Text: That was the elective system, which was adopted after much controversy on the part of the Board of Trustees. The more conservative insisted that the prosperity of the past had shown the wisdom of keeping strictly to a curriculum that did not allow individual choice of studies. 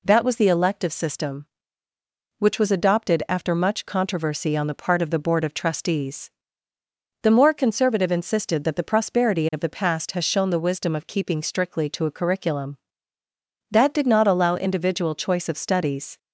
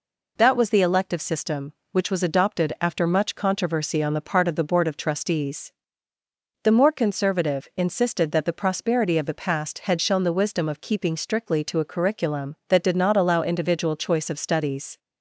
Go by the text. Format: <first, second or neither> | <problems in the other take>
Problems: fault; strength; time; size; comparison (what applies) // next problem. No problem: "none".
second | says "has" for "had"; at 10.1 s